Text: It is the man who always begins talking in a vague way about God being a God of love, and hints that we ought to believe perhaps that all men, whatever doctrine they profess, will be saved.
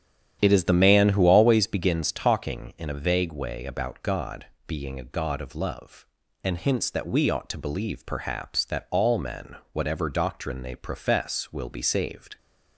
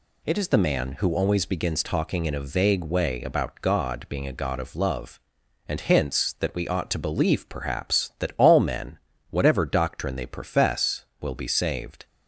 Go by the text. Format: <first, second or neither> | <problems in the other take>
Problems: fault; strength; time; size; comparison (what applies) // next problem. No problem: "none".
second | starts louder than the rest; strong; until 1.8 s; 9.5 dB // pauses between "God" and "being"; slight; at 4.4 s; 0.22 s long